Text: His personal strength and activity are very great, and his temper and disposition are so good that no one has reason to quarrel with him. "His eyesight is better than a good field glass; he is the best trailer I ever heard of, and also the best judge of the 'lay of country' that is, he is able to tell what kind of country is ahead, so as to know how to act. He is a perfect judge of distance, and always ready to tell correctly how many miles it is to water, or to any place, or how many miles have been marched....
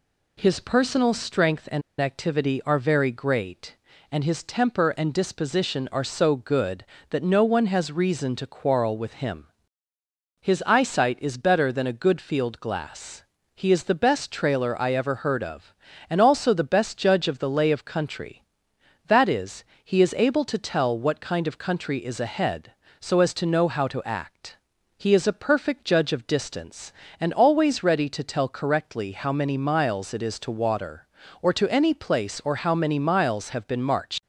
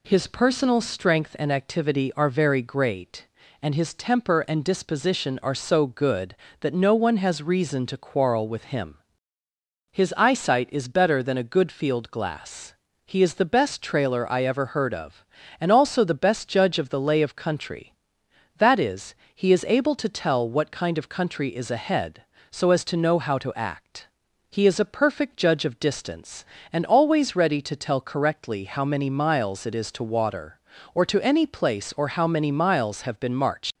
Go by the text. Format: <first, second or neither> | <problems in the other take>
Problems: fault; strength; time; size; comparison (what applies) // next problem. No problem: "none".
second | pauses between "and" and "activity"; slight; at 1.8 s; 0.19 s long